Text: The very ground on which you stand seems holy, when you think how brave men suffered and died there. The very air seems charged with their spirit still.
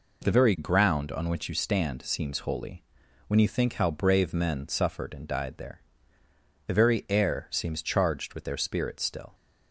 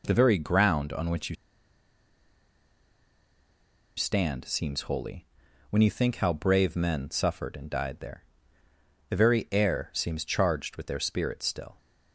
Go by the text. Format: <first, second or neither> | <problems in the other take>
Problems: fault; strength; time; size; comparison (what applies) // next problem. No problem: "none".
first | pauses between "you" and "stand"; strong; at 1.3 s; 2.6 s long